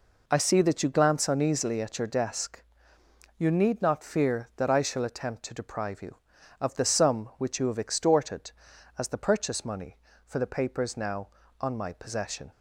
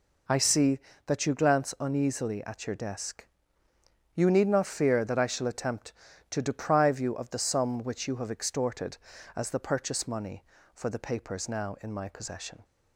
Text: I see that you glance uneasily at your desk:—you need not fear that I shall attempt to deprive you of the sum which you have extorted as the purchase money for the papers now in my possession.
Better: second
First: says "on" for "in"; at 11.5 s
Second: none

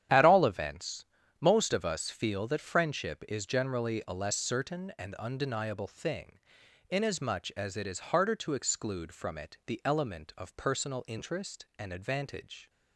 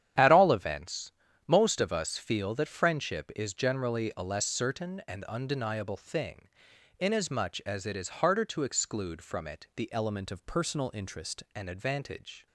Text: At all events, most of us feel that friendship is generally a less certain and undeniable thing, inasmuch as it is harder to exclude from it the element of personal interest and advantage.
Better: first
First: starts louder than the rest; strong; until 1.4 s; 10 dB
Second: starts louder than the rest; strong; until 1.5 s; 10 dB // changes voice from "element" to "interest"; from 9.9 to 11.4 s; 1.5 s long

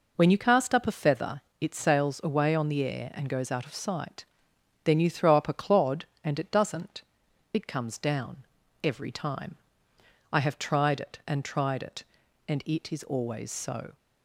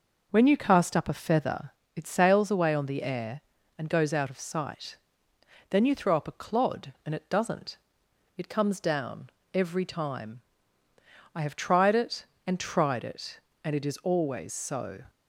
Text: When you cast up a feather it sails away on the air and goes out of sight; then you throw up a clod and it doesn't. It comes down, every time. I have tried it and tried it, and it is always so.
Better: neither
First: pauses between "feather" and "it"; slight; at 1.4 s; 0.18 s long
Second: pauses between "feather" and "it"; slight; at 1.7 s; 0.24 s long

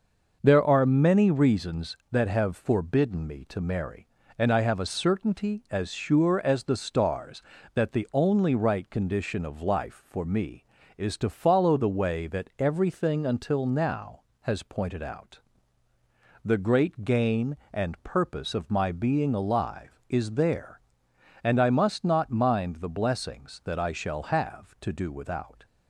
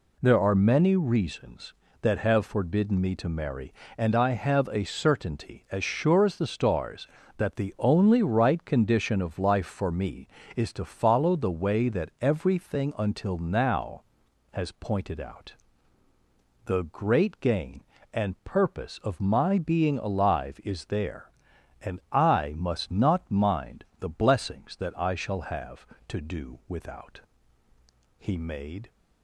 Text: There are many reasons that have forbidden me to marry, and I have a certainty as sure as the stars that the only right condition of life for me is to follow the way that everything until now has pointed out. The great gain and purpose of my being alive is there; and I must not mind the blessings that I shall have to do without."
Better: first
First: none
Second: goes on to say "He made"; noticeable; from 28.1 s on; 0.72 s long

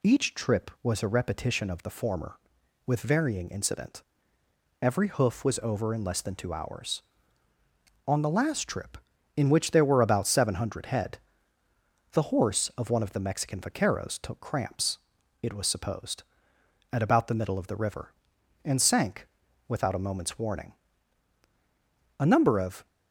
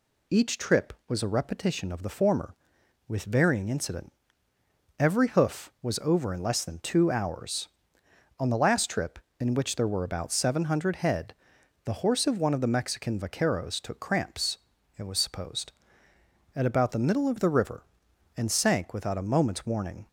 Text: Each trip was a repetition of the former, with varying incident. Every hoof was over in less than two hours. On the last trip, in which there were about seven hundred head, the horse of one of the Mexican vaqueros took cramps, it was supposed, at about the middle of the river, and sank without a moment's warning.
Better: second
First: pauses between "sank" and "without"; at 19.2 s; 0.40 s long // goes on to say "A number of"; noticeable; from 22.1 s on; 0.68 s long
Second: none

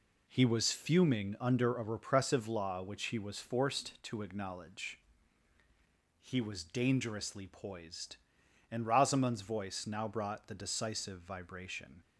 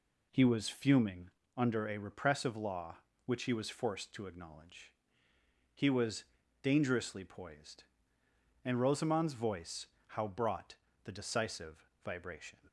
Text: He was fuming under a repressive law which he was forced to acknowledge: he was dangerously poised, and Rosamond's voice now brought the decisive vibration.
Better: first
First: none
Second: pauses between "fuming" and "under"; slight; at 1.2 s; 0.28 s long // pauses between "was" and "dangerously"; at 6.2 s; 0.40 s long // says "how" for "now"; at 10.0 s // pauses between "brought" and "the"; slight; at 10.7 s; 0.26 s long // pauses between "decisive" and "vibration"; slight; at 11.8 s; 0.16 s long

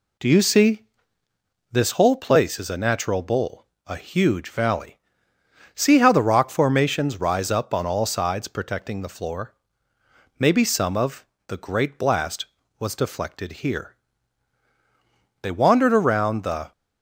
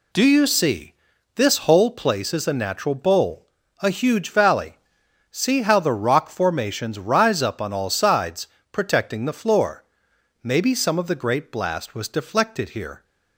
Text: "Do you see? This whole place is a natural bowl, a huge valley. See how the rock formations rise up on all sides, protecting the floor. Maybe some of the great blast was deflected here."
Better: second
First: pauses between "of" and "the"; slight; at 11.2 s; 0.22 s long // goes on to say "They wandered around the"; noticeable; from 15.4 s on; 1.3 s long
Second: none

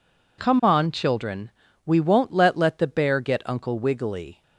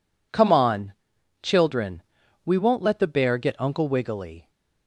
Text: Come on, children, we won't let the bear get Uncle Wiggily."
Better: second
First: says "let" twice; at 2.5 s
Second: none

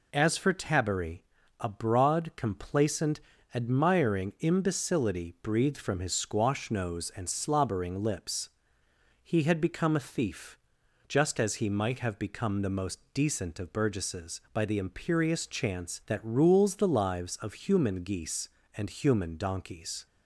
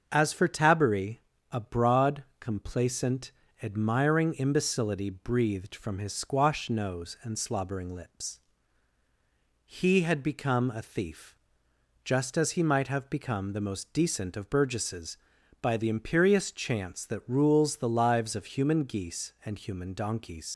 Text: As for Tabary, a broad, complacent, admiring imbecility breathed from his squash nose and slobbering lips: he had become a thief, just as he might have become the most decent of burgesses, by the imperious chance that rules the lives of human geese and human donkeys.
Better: first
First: none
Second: starts louder than the rest; until 1.1 s; 6.5 dB // leaves "donkeys" unfinished; at 20.5 s; 90 ms

